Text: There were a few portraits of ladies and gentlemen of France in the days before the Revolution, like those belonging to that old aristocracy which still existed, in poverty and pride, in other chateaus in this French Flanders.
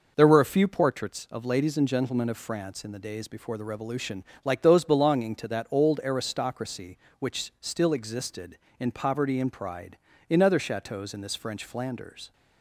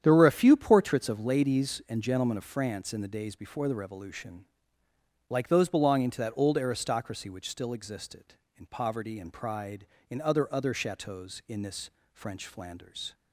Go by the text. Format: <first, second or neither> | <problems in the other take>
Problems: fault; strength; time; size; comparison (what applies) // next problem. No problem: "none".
first | starts louder than the rest; strong; until 1.0 s; 9 dB // says "other" twice; at 10.5 s // pauses between "this" and "French"; slight; at 11.9 s; 0.22 s long